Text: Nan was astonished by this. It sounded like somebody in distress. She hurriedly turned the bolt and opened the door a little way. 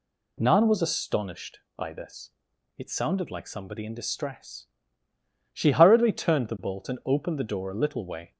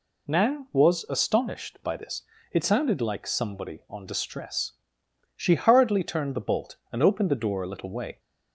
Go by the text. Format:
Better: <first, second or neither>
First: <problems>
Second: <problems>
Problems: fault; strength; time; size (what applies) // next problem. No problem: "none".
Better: first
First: none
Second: says "on" for "in"; at 3.8 s